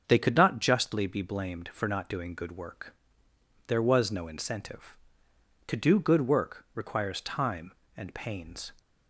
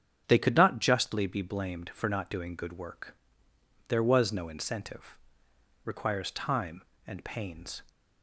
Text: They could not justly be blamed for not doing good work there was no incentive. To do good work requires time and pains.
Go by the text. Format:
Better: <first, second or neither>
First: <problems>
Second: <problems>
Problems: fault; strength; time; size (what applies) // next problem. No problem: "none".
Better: first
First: starts louder than the rest; until 1.0 s; 6.5 dB // pauses between "work" and "there"; noticeable; at 2.9 s; 0.74 s long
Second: starts louder than the rest; strong; until 1.2 s; 8 dB // pauses between "work" and "there"; noticeable; at 3.1 s; 0.74 s long // skips "To do good work"; at 5.5 s